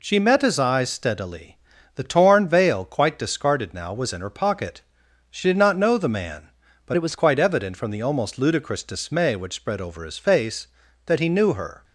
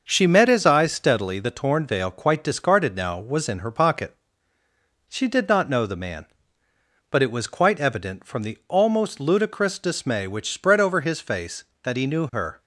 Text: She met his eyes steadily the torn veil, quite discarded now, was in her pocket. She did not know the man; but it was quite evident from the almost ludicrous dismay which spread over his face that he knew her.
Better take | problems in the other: second | pauses between "steadily" and "the"; slight; at 1.5 s; 0.36 s long // changes voice from "it" to "was"; from 6.9 to 7.1 s; 0.2 s long

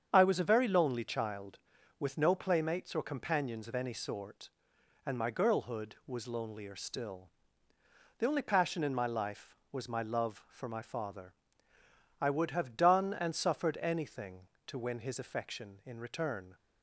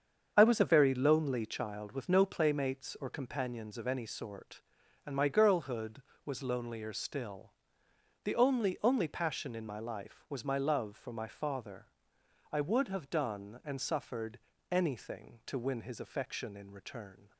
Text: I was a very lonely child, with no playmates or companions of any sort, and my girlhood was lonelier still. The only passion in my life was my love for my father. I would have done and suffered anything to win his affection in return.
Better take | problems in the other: first | starts louder than the rest; strong; until 1.3 s; 7 dB; strong in the first // says "only" twice; at 8.8 s // pauses between "suffered" and "anything"; slight; at 14.3 s; 0.32 s long

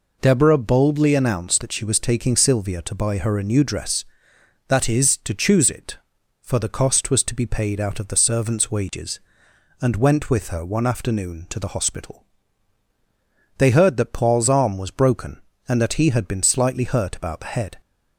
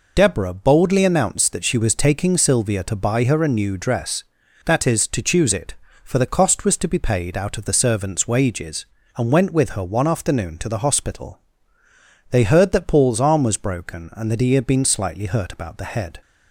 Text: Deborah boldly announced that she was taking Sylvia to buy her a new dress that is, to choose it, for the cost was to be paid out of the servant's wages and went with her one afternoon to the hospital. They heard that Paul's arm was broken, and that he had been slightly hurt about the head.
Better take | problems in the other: first | loses the start of "Deborah"; at 0.1 s; 40 ms

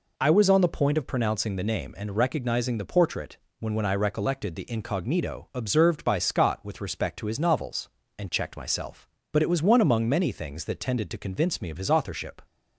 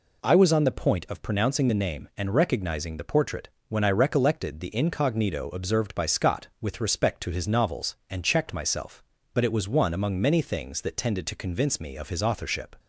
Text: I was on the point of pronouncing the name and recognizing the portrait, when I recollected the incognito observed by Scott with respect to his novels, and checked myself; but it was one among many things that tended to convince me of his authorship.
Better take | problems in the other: second | says "when" twice; at 3.7 s

